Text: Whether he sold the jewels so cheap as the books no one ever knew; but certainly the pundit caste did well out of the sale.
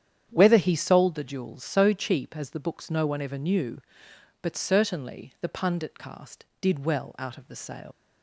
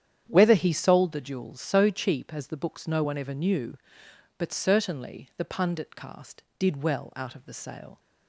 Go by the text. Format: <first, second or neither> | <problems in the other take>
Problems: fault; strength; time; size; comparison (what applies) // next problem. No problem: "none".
second | starts louder than the rest; strong; until 1.3 s; 9.5 dB; strong in the second // leaves "sale" unfinished; at 7.9 s; 105 ms